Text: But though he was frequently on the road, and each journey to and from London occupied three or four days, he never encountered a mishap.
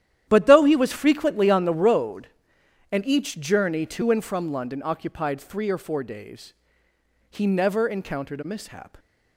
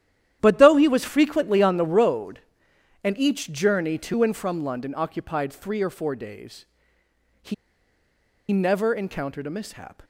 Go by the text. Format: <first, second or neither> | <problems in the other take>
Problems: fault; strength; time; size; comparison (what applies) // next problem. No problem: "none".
first | starts louder than the rest; strong; until 1.4 s; 11 dB; strong in the first // pauses between "he" and "never"; noticeable; at 7.5 s; 0.97 s long